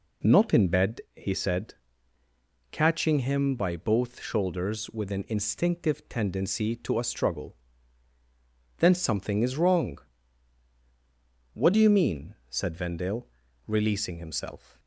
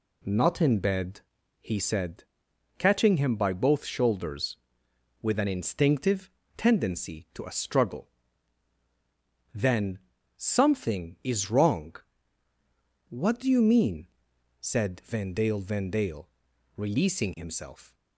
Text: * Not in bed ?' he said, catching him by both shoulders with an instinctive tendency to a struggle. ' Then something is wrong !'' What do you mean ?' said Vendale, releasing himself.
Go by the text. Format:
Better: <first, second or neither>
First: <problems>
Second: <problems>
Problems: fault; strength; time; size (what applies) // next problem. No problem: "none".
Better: first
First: none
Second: pauses between "instinctive" and "tendency"; slight; at 6.2 s; 0.28 s long // pauses between "Then" and "something"; at 9.9 s; 0.40 s long // says "Vendale" twice; at 15.5 s